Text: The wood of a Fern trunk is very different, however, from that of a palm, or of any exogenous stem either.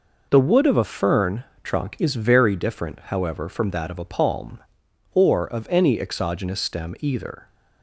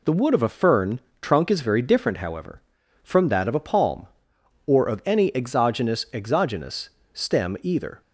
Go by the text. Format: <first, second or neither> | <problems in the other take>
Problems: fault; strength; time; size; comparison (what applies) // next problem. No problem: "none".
first | pauses between "Fern" and "trunk"; slight; at 0.9 s; 0.22 s long; slight in the first // says "exogenous" twice; at 6.1 s